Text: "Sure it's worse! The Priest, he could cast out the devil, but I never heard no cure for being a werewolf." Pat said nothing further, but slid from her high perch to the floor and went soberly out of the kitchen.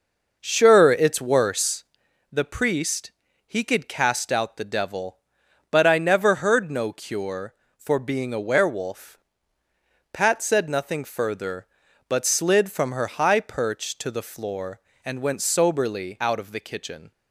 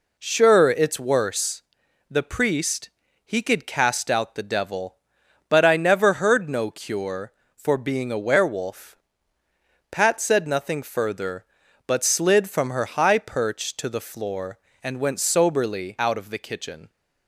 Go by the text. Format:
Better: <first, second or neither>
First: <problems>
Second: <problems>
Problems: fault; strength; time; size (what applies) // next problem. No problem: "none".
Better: second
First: starts louder than the rest; noticeable; until 2.2 s; 5.5 dB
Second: none